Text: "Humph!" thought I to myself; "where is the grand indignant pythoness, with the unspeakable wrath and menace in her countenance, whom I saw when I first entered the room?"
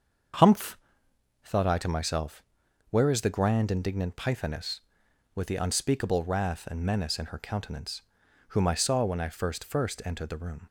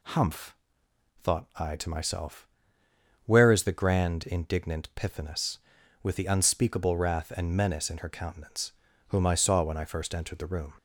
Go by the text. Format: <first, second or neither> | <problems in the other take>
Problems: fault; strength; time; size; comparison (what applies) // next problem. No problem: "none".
second | starts louder than the rest; until 2.0 s; 7 dB // says "first" twice; at 9.6 s